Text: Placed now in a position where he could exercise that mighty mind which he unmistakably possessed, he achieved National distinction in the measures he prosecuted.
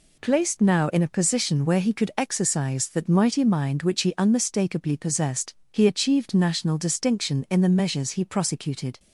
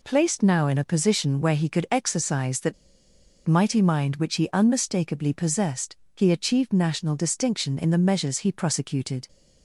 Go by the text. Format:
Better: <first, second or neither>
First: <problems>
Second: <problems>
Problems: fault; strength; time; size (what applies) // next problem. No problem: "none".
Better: first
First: none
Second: pauses between "that" and "mighty"; noticeable; at 2.7 s; 0.73 s long